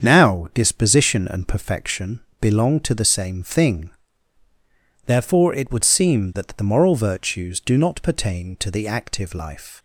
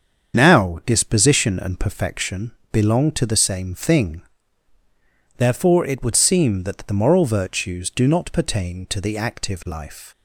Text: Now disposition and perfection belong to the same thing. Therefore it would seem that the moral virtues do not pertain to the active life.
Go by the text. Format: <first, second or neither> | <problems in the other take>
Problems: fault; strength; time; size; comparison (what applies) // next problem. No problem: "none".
first | loses the start of "Now"; at 0.3 s; 25 ms // starts louder than the rest; strong; until 1.4 s; 7 dB; strong in the first // pauses between "perfection" and "belong"; slight; at 2.5 s; 0.20 s long; slight in the first